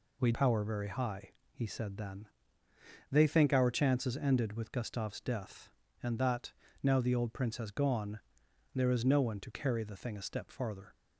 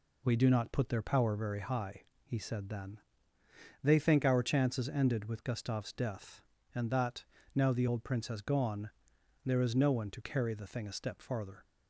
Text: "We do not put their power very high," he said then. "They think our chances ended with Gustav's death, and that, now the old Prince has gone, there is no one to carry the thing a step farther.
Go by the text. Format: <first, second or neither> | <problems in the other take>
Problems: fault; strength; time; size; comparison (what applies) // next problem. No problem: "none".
second | skips "do not put their"; at 0.3 s